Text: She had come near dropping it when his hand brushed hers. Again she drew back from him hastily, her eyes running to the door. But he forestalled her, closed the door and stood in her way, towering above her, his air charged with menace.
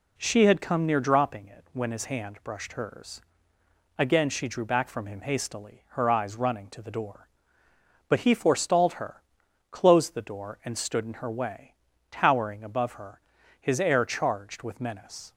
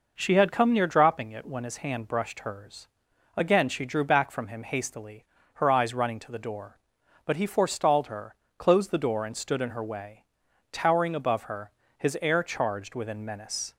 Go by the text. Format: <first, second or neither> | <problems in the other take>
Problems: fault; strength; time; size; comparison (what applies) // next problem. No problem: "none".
first | says "within" for "with"; at 12.9 s